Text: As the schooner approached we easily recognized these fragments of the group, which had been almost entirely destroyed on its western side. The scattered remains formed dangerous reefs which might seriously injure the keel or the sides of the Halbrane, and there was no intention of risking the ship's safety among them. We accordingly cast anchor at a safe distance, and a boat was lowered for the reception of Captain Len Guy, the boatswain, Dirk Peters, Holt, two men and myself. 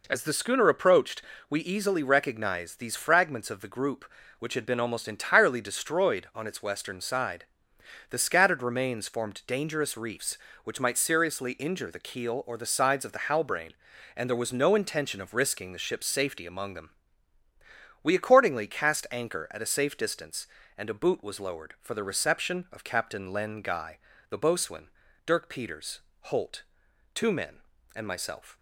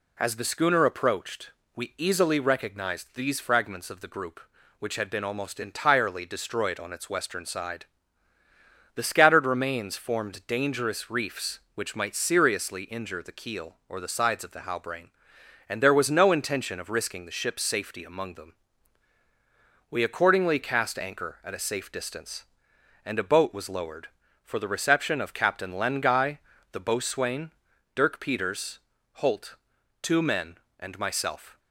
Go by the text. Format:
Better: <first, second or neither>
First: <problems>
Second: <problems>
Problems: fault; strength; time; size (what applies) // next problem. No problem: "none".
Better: second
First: pauses between "approached" and "we"; slight; at 1.2 s; 0.28 s long // says "boot" for "boat"; at 20.9 s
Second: pauses between "approached" and "we"; slight; at 1.5 s; 0.24 s long